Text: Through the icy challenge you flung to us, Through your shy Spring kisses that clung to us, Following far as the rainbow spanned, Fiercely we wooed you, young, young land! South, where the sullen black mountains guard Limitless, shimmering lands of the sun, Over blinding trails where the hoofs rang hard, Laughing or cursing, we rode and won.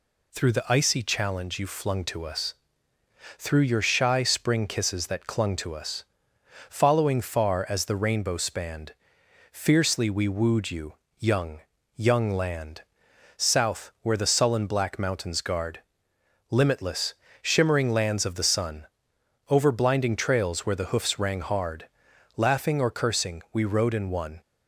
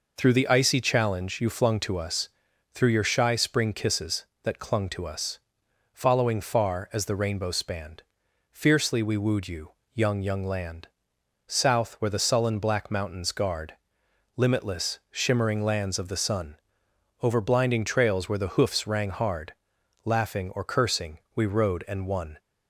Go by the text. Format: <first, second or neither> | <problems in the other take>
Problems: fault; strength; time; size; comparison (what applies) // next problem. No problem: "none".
neither | pauses between "guard" and "Limitless"; noticeable; the same in both